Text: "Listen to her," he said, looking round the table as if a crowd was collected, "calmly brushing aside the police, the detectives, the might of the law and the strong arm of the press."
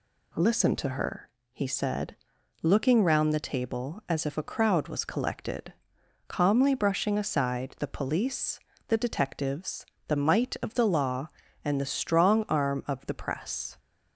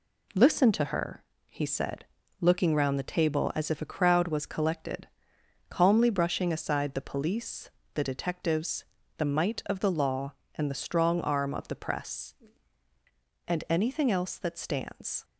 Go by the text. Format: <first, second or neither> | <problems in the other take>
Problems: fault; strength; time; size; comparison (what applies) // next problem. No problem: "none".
first | goes on to say "And anything else that stands"; strong; from 13.4 s on; 1.7 s long